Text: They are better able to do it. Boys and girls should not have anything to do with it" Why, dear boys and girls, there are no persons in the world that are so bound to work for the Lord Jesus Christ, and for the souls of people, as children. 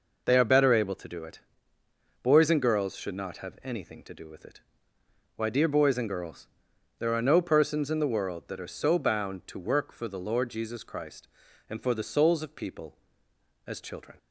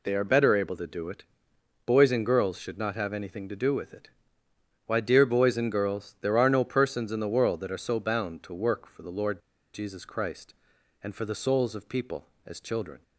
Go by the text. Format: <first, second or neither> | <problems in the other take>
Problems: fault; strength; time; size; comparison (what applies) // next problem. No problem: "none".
first | pauses between "it" and "Why"; noticeable; at 4.0 s; 0.78 s long; noticeable in the first // pauses between "Lord" and "Jesus"; slight; at 9.4 s; 0.33 s long